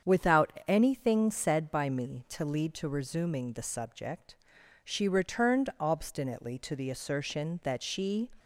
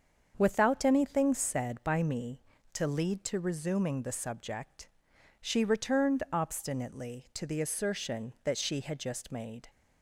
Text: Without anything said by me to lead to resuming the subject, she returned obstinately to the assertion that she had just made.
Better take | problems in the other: second | starts louder than the rest; strong; until 1.2 s; 7.5 dB; also in the second // pauses between "Without" and "anything"; slight; at 0.5 s; 0.16 s long // stops before "had just made"; at 8.3 s

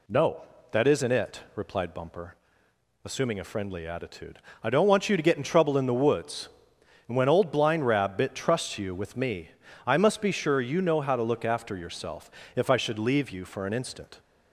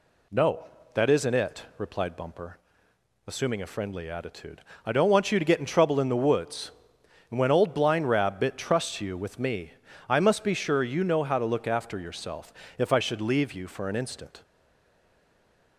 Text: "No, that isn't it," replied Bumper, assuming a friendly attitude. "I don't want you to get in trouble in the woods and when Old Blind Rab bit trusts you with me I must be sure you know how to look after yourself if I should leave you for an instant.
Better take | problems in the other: first | pauses between "me" and "I"; slight; at 9.7 s; 0.36 s long; slight in the first // pauses between "yourself" and "if"; slight; at 12.5 s; 0.24 s long; slight in the first // stays silent after the last word; noticeable; from 14.4 s on; 1.3 s long

